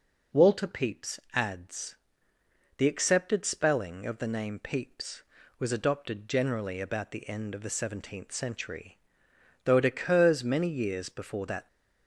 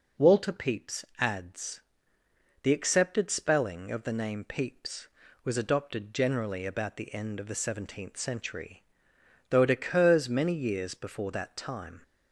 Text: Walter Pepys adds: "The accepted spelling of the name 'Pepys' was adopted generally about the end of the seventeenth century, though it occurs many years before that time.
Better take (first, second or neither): second